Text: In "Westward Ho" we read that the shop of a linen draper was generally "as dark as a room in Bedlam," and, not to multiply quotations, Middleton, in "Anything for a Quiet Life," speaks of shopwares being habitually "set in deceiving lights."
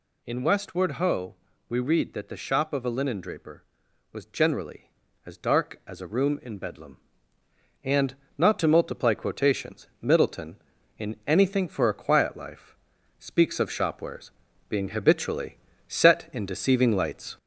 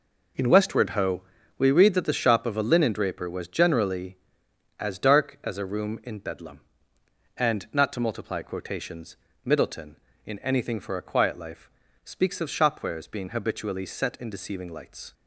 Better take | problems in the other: second | gets louder; slight; throughout; 2 dB // pauses between "Ho" and "we"; slight; at 1.3 s; 0.34 s long; slight in the second // pauses between "shopwares" and "being"; at 14.2 s; 0.40 s long // pauses between "habitually" and "set"; slight; at 15.5 s; 0.30 s long

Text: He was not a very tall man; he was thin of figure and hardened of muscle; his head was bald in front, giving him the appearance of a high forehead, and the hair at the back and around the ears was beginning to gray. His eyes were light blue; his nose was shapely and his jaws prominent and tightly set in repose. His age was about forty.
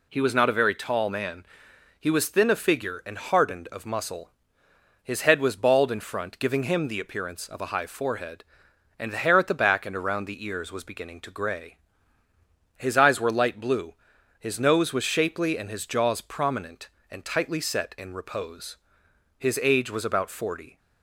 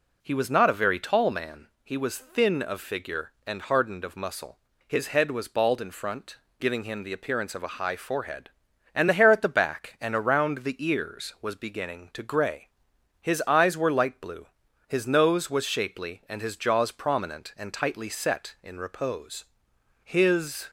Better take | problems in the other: first | stops before "age was about forty"; at 20.6 s

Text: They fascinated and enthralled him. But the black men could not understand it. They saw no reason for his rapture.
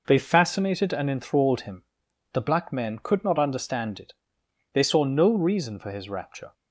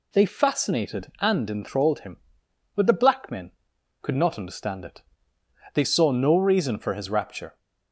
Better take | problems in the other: second | skips "But"; at 2.0 s

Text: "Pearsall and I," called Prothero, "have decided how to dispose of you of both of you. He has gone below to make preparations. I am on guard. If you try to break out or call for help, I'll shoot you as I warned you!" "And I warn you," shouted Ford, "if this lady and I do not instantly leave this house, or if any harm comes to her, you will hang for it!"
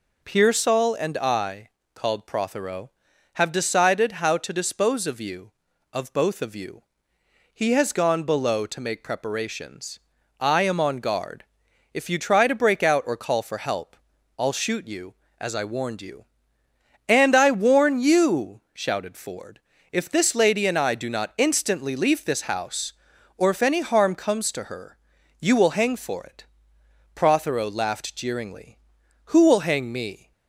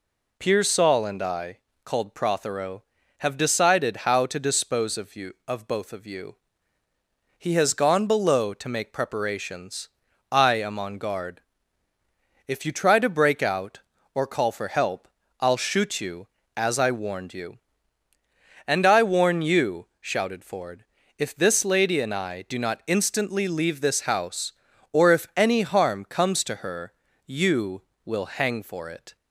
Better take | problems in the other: second | goes on to say "Prothero laughed jeeringly Who will hang me"; strong; from 27.1 s on; 3.1 s long

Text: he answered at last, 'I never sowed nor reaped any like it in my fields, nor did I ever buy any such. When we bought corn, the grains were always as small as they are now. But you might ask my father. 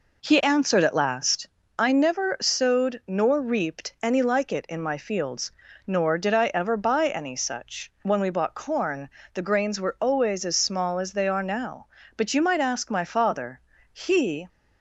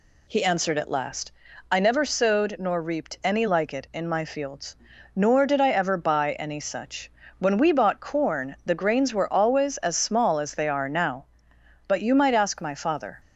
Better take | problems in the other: second | goes on to say "He"; from 13.9 s on; 0.56 s long

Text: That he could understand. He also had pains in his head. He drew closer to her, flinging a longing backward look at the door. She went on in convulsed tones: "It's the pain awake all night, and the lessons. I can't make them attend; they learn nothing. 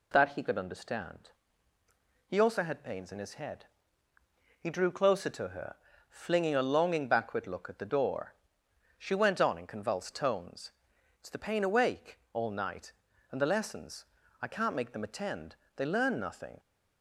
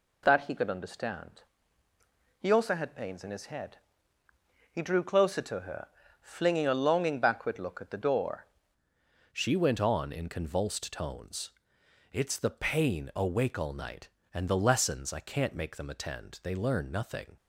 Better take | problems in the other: first | changes voice at "She"; from 9.3 s on; 8.0 s long

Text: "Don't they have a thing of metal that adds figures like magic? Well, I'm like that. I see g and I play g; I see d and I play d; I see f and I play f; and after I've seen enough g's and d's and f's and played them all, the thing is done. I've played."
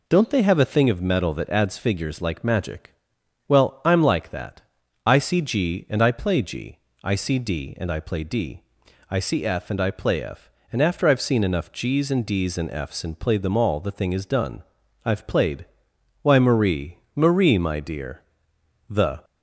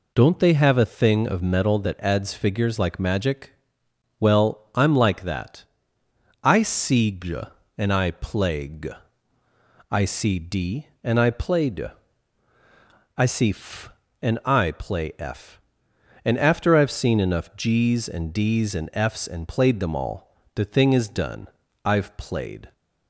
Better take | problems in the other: second | goes on to say "Why Marie Marie my dear The"; strong; from 16.2 s on; 3.0 s long

